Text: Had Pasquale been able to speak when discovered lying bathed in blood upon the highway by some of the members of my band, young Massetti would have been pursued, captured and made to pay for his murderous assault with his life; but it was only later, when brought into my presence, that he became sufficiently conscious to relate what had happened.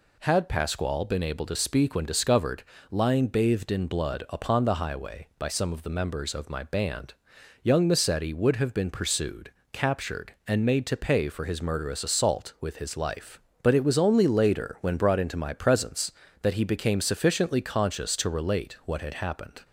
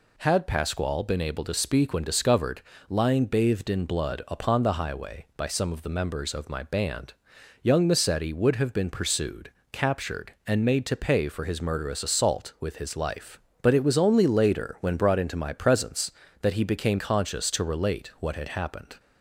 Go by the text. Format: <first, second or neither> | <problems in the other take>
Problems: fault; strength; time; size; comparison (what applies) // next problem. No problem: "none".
first | pauses between "discovered" and "lying"; slight; at 2.6 s; 0.26 s long; slight in the first // skips "sufficiently"; at 16.9 s